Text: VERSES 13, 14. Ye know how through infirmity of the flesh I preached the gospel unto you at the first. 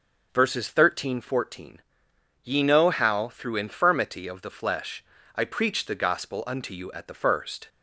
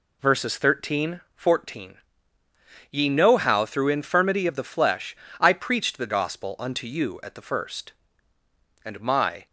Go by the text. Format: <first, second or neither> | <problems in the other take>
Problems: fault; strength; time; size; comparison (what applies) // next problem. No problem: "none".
first | pauses between "flesh" and "I"; slight; at 5.1 s; 0.23 s long; slight in the first // goes on to say "And my"; noticeable; from 8.8 s on; 0.62 s long